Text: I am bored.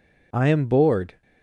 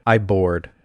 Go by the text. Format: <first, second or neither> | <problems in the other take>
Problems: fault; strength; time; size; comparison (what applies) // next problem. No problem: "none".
first | skips "am"; at 0.1 s